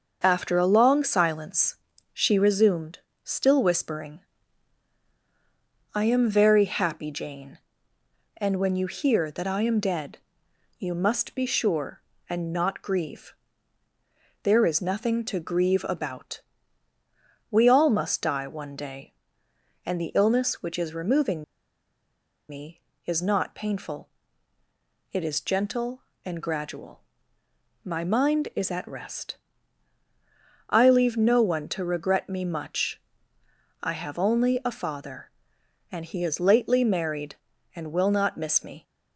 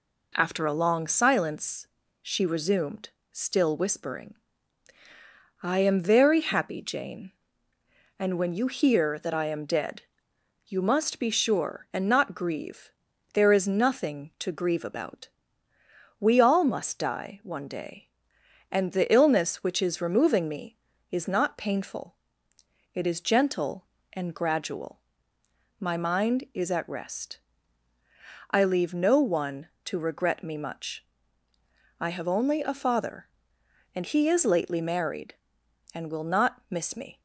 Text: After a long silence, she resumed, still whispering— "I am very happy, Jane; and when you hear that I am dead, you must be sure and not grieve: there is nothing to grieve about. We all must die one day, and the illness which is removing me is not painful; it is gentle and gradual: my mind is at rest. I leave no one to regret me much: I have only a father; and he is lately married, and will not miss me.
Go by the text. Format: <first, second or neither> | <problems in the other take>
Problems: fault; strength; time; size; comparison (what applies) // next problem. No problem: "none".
second | starts louder than the rest; until 1.2 s; 6.5 dB // pauses between "removing" and "me"; at 21.4 s; 1.0 s long